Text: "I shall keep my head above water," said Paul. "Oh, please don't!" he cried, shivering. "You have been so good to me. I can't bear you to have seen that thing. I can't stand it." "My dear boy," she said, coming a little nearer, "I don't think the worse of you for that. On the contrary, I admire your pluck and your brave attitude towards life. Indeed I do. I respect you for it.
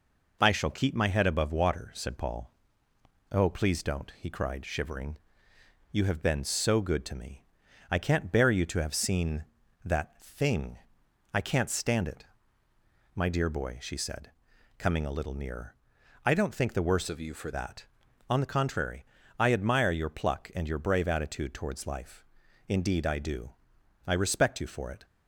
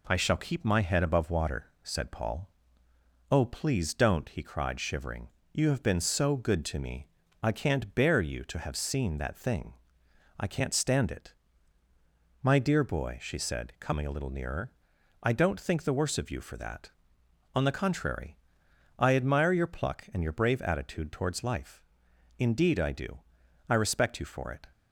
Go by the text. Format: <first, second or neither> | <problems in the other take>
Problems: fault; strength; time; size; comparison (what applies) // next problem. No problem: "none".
second | changes voice from "of" to "for"; from 17.0 to 17.5 s; 0.5 s long